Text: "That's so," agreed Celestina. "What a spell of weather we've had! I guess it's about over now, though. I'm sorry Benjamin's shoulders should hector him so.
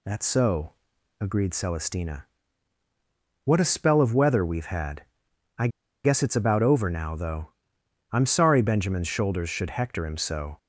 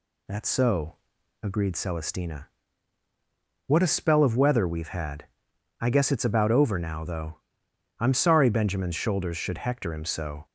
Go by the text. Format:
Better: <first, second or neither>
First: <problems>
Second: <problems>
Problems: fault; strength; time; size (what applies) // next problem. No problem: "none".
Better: second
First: pauses between "I" and "guess"; at 5.6 s; 0.36 s long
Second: none